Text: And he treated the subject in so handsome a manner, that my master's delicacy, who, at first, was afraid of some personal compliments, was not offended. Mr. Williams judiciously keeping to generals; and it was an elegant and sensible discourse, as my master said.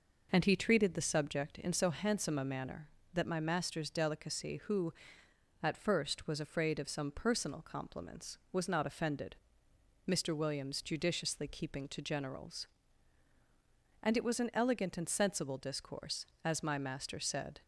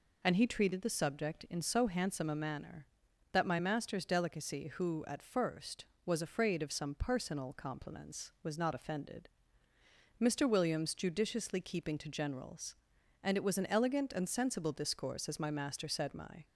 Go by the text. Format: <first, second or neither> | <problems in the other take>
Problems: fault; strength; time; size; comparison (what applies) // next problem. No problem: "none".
first | goes on to say "My"; slight; from 16.1 s on; 0.30 s long